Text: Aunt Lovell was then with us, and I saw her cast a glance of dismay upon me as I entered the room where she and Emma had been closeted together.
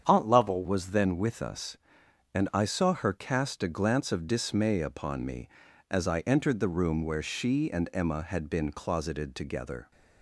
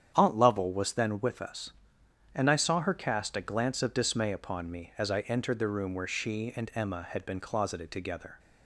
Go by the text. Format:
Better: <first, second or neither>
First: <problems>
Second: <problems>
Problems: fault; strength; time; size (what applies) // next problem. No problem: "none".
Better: second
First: starts louder than the rest; strong; until 1.0 s; 8 dB // changes voice at "was"; from 0.6 s on; 9.3 s long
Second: starts louder than the rest; strong; until 1.1 s; 9 dB